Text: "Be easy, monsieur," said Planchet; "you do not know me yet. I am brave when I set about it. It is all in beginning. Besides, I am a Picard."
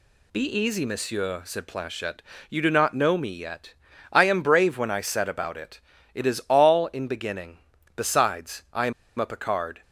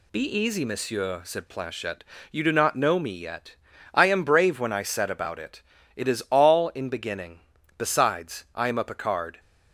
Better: second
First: pauses between "am" and "a"; slight; at 8.9 s; 0.26 s long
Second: none

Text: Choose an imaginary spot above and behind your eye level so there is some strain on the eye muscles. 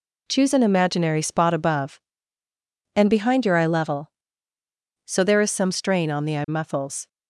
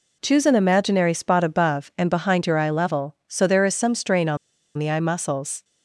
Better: first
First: none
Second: pauses between "on" and "the"; at 4.3 s; 0.40 s long

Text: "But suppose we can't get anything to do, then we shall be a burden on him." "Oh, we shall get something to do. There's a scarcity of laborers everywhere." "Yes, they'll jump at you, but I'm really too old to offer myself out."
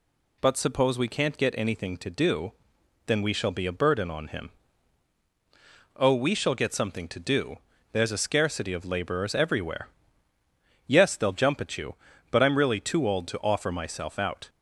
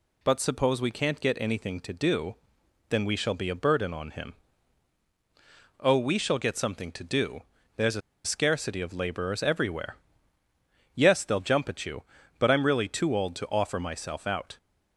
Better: first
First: none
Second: pauses between "a" and "scarcity"; slight; at 8.0 s; 0.24 s long

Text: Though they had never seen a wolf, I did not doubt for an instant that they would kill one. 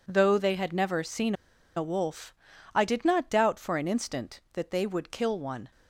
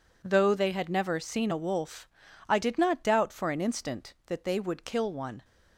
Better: second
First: pauses between "seen" and "a"; at 1.3 s; 0.42 s long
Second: none

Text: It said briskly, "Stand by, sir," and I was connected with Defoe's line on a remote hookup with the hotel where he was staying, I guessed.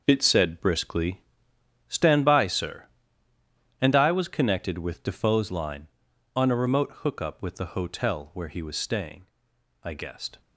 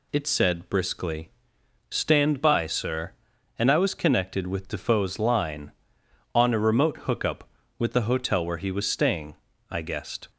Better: second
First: gets quieter; strong; throughout; 10 dB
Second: none

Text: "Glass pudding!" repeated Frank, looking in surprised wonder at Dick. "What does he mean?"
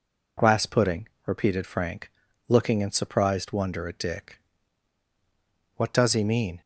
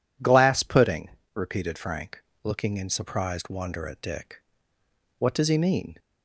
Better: neither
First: none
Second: none

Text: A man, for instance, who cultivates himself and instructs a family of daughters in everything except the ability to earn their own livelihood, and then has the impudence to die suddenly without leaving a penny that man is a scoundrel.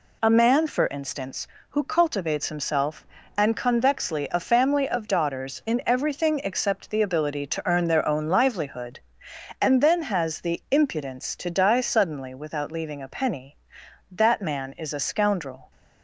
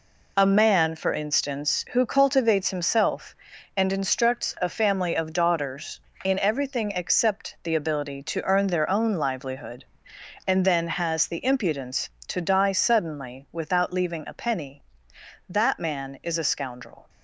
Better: second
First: says "convexly" for "instructs"; at 3.5 s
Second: none

